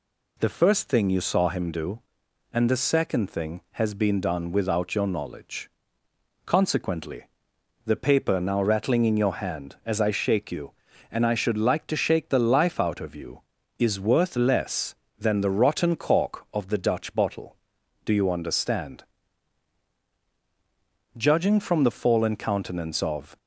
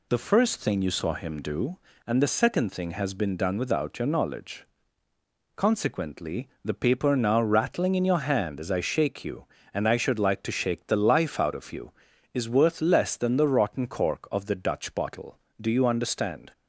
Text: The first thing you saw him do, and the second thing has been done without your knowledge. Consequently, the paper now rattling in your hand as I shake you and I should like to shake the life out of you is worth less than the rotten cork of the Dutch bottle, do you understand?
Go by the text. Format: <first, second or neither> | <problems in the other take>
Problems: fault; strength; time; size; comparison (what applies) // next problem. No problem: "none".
second | goes on to say "Judging from the fallen countenance of"; strong; from 21.1 s on; 2.2 s long